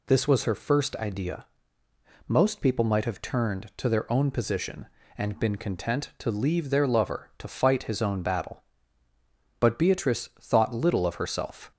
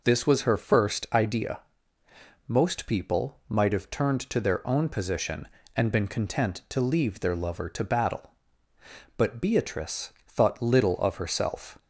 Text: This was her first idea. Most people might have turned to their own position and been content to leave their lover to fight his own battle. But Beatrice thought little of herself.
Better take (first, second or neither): first